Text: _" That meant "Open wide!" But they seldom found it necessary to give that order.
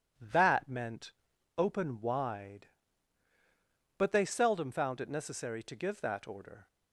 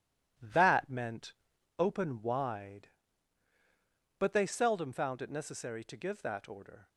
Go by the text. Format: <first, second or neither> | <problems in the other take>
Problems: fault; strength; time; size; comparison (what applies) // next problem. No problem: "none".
first | gets quieter; noticeable; throughout; 6 dB // pauses between "meant" and "Open"; noticeable; at 1.3 s; 0.46 s long; noticeable in the first